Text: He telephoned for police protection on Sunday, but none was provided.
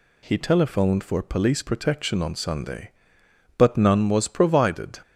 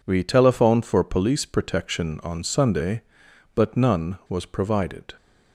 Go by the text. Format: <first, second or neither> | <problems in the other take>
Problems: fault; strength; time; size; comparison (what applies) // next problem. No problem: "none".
first | says "We" for "He"; at 0.0 s